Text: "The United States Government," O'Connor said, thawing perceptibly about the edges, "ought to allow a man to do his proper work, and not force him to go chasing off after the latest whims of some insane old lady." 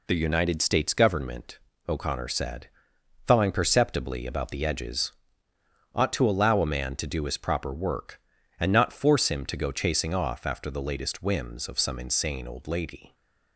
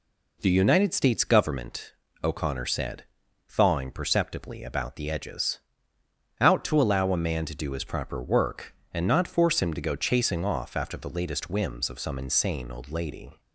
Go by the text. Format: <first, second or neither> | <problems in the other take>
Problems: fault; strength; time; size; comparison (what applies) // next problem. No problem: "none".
first | says "out" for "ought"; at 6.3 s